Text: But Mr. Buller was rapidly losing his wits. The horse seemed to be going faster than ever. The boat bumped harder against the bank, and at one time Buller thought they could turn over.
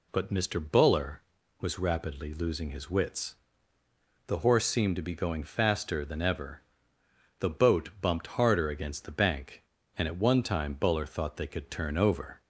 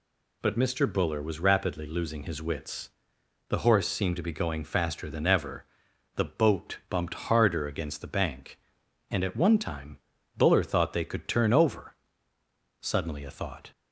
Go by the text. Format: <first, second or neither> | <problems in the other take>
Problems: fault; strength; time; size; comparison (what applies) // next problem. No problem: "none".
first | pauses between "time" and "Buller"; at 9.9 s; 0.38 s long // goes on to say "Suddenly a thought"; noticeable; from 12.8 s on; 0.90 s long